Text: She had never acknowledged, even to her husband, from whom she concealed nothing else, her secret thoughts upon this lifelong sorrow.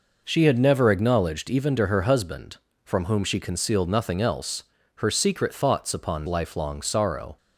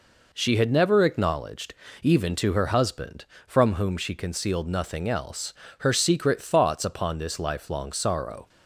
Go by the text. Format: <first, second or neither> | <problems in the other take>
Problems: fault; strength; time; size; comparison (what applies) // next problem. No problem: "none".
second | skips "this"; at 6.2 s